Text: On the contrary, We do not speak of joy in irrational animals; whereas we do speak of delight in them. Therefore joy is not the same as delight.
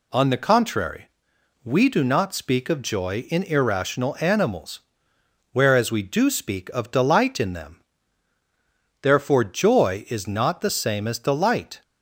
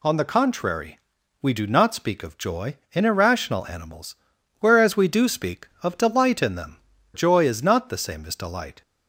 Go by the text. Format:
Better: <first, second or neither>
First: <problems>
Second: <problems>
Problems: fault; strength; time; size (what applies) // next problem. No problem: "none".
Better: first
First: none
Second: skips "Therefore"; at 6.9 s